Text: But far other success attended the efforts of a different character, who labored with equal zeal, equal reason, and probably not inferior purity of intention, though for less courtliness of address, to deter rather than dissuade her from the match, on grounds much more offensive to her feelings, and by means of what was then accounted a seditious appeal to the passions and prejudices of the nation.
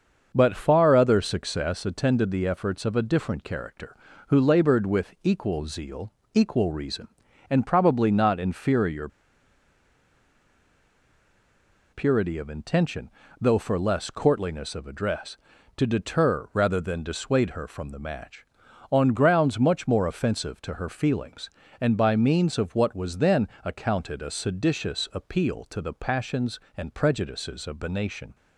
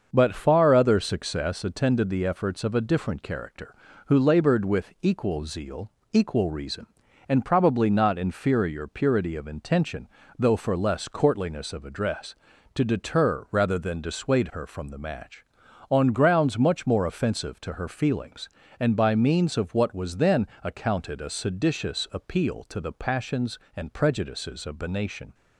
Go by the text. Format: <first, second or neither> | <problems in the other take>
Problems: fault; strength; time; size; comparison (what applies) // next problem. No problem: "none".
second | starts louder than the rest; until 1.3 s; 6.5 dB; also in the second // pauses between "inferior" and "purity"; strong; at 9.0 s; 2.8 s long // pauses between "then" and "accounted"; slight; at 23.4 s; 0.18 s long; slight in the second